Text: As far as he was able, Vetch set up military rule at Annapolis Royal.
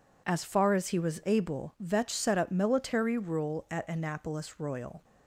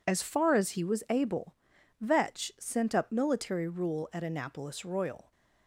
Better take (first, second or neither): first